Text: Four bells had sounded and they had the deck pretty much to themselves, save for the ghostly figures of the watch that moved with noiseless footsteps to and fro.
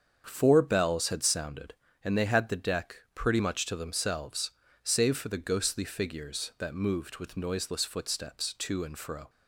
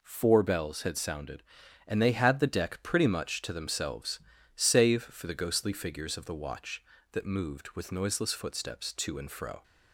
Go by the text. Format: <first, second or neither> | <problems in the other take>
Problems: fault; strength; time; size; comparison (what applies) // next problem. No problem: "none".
second | starts louder than the rest; strong; until 1.2 s; 7 dB // pauses between "deck" and "pretty"; slight; at 2.9 s; 0.18 s long // skips "of the watch"; at 6.5 s